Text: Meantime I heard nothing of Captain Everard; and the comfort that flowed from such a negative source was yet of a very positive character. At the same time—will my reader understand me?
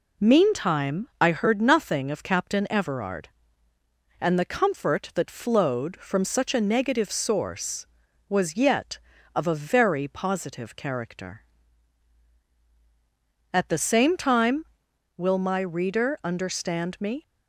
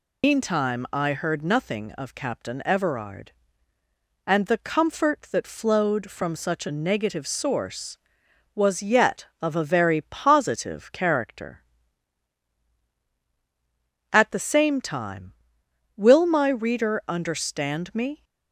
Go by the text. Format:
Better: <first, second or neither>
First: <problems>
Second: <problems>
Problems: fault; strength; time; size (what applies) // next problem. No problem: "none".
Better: first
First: none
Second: loses the start of "Meantime"; at 0.2 s; 100 ms